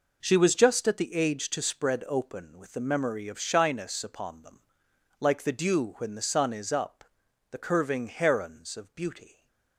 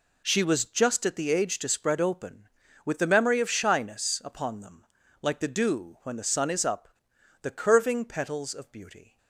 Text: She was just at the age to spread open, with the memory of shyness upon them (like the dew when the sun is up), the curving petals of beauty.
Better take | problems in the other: second | says "herons" for "petals"; at 8.0 s // stays silent after the last word; slight; from 9.2 s on; 0.5 s long

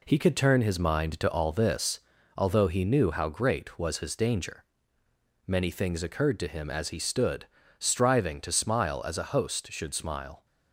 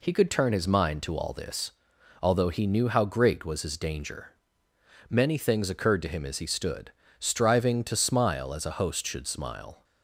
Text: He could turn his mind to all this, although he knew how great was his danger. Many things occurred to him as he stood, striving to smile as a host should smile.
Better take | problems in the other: second | gets quieter; noticeable; throughout; 5 dB

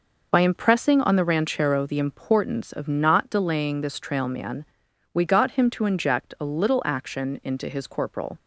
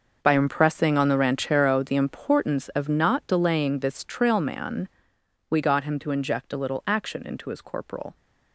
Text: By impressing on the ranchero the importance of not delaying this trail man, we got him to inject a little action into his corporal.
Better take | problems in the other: first | gets quieter; strong; throughout; 13.5 dB

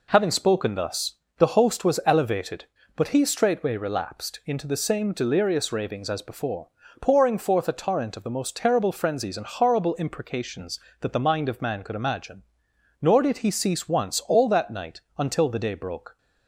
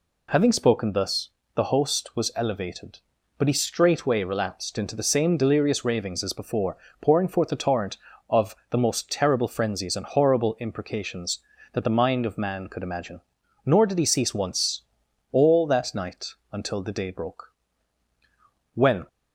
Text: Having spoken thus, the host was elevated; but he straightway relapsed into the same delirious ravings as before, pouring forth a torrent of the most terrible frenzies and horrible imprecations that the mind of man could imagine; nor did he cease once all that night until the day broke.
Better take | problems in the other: first | pauses between "once" and "all"; noticeable; at 14.8 s; 0.50 s long // pauses between "night" and "until"; slight; at 16.3 s; 0.16 s long // goes on to say "When"; slight; from 18.7 s on; 0.32 s long

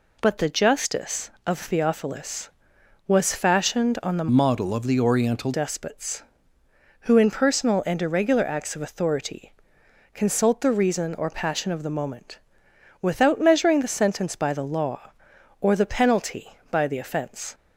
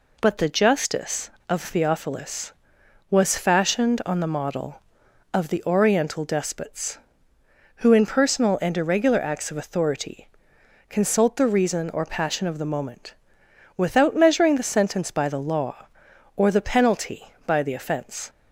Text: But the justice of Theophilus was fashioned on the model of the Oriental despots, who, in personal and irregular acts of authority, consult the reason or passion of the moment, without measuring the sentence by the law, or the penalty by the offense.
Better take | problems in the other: second | changes voice from "model" to "Oriental"; from 4.2 to 5.5 s; 1.3 s long

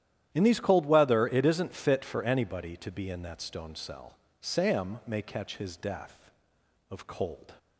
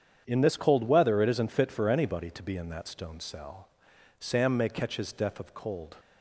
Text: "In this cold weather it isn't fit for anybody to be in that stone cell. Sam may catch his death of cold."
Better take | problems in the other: second | starts louder than the rest; strong; until 1.3 s; 11.5 dB; strong in the second // says "these" for "this"; at 0.4 s

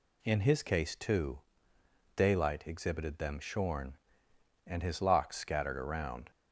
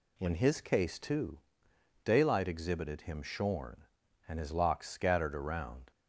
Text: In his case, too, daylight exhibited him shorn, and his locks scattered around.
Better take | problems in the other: second | says "them" for "him"; at 3.1 s

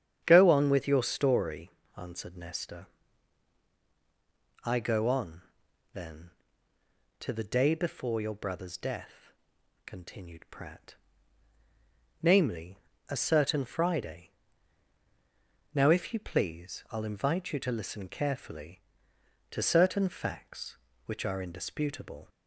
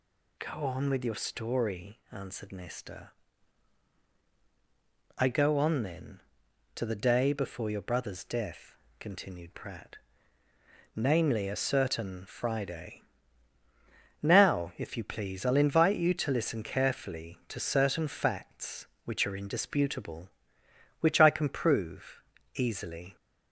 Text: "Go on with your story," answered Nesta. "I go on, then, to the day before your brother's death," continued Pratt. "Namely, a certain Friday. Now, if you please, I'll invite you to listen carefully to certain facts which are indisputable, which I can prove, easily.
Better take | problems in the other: second | starts louder than the rest; strong; until 1.2 s; 9 dB // stops before "which I can prove easily"; at 22.2 s

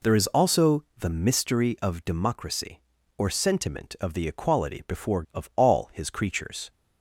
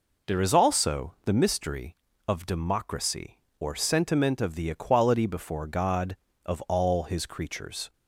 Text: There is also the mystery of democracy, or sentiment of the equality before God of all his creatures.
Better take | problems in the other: second | skips "God"; at 5.2 s

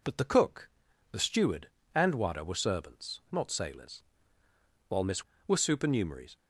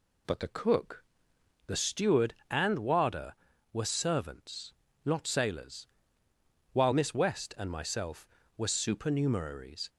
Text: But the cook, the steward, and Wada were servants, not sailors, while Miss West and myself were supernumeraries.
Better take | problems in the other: second | skips "West and myself"; at 5.3 s

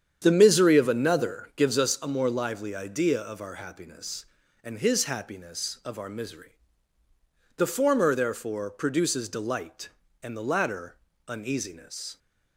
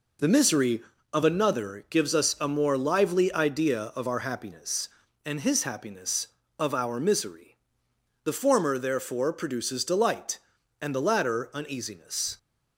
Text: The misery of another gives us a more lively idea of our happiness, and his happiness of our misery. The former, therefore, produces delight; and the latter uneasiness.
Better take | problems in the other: second | starts louder than the rest; strong; until 1.9 s; 8.5 dB // pauses between "latter" and "uneasiness"; slight; at 10.9 s; 0.28 s long

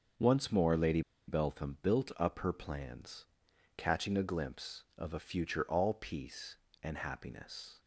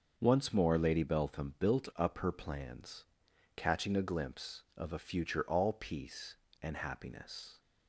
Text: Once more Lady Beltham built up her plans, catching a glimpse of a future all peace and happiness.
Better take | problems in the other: second | starts louder than the rest; until 1.4 s; 6.5 dB; also in the second // pauses between "Lady" and "Beltham"; slight; at 1.0 s; 0.26 s long

